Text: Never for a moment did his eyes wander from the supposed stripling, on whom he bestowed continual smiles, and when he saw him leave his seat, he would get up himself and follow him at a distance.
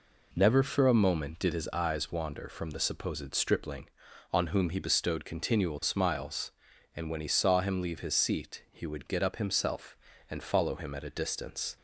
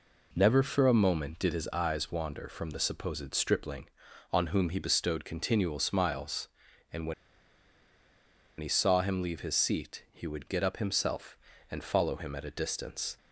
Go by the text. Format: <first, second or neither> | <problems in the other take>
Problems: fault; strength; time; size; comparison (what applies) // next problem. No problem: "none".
first | pauses between "when" and "he"; strong; at 7.1 s; 1.4 s long